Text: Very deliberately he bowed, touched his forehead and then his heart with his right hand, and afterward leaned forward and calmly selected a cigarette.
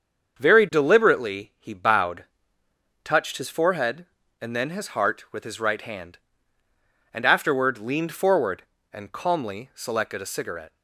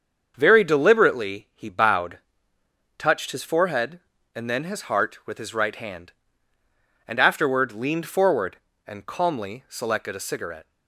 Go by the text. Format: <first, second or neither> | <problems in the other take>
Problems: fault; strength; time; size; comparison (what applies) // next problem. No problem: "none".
neither | starts louder than the rest; the same in both